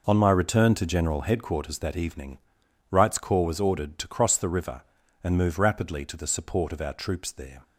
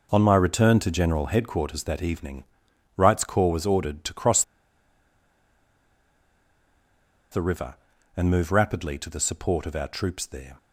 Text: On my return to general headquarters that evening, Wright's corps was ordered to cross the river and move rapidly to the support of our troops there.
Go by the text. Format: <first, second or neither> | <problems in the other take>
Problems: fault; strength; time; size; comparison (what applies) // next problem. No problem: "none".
first | pauses between "cross" and "the"; strong; at 4.4 s; 2.8 s long